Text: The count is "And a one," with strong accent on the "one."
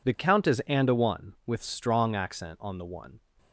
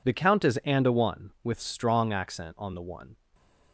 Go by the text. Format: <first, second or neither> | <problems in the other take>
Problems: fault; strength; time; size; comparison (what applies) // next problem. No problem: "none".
neither | none